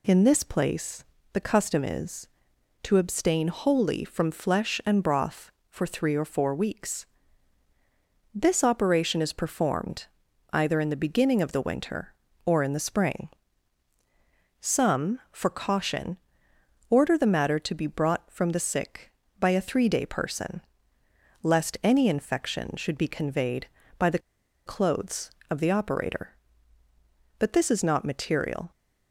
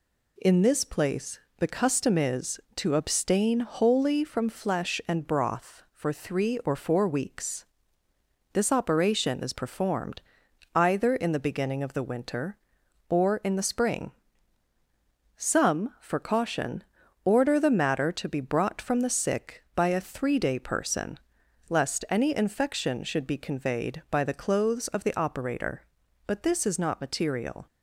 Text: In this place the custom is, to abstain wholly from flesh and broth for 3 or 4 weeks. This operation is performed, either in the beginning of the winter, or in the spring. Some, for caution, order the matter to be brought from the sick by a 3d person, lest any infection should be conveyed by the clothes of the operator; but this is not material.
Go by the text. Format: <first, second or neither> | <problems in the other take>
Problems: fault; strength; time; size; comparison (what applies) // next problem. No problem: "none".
second | pauses between "place" and "the"; slight; at 1.0 s; 0.30 s long; slight in the second // pauses between "the" and "clothes"; noticeable; at 24.2 s; 0.47 s long